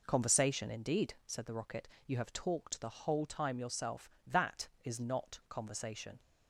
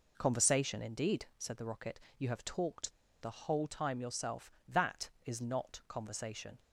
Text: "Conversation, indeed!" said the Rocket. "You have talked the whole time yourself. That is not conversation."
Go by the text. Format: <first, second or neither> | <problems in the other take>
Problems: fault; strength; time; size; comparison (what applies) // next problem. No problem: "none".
first | pauses between "talked" and "the"; slight; at 2.9 s; 0.31 s long